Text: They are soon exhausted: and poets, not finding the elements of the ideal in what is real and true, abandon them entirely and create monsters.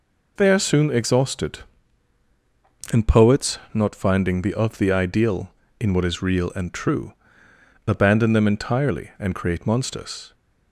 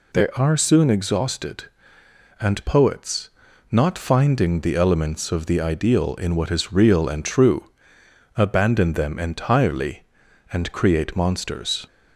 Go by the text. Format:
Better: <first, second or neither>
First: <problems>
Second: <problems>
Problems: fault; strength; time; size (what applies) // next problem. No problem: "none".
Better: second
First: skips "elements"; at 4.5 s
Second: none